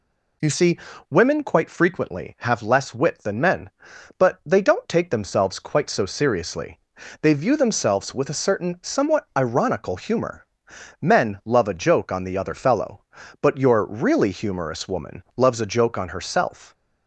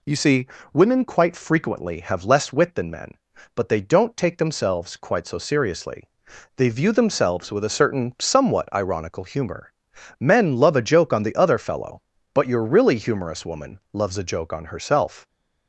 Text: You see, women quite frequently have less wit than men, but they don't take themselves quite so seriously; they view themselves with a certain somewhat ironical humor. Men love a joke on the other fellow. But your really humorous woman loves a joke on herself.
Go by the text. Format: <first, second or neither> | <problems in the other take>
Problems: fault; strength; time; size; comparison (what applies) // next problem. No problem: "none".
neither | none